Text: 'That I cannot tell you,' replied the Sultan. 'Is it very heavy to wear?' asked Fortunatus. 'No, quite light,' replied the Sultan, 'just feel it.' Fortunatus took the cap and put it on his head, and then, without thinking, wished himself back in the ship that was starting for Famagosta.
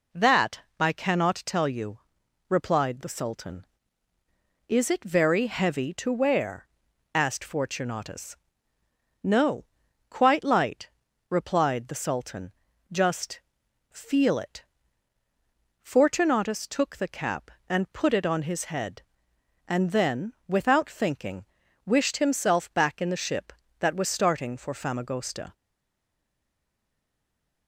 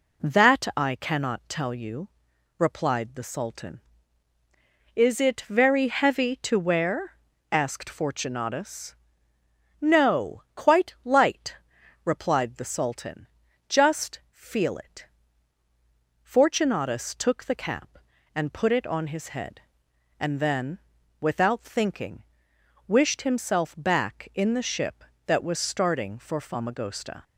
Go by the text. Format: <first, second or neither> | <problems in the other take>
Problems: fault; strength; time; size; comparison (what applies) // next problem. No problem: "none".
second | pauses between "That" and "I"; slight; at 0.6 s; 0.18 s long // pauses between "just" and "feel"; noticeable; at 13.3 s; 0.50 s long // stays silent after the last word; from 25.5 s on; 2.1 s long